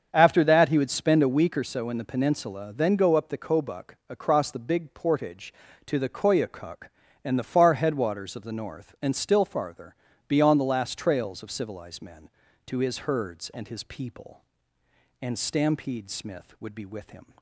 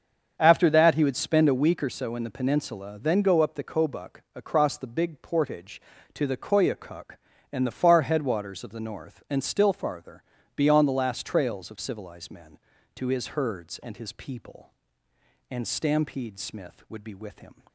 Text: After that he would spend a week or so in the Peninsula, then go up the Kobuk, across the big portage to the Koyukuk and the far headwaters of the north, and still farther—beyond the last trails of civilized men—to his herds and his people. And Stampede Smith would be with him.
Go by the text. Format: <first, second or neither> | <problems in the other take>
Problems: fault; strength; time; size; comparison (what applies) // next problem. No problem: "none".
neither | starts louder than the rest; strong; the same in both